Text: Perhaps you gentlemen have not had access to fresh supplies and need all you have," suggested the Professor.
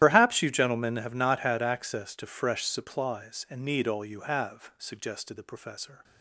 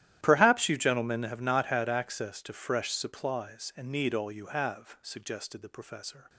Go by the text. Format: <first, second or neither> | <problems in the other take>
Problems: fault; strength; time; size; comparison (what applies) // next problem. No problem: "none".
second | loses the start of "Perhaps"; at 0.0 s; 65 ms // starts louder than the rest; strong; until 1.0 s; 12.5 dB; strong in the second